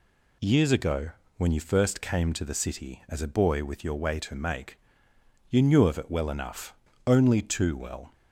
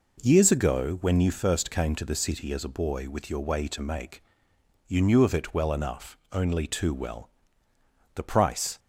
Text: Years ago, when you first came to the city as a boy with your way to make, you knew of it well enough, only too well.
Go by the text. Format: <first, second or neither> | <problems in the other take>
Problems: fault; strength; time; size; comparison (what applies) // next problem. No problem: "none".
first | goes on to say "The price"; noticeable; from 8.1 s on; 0.64 s long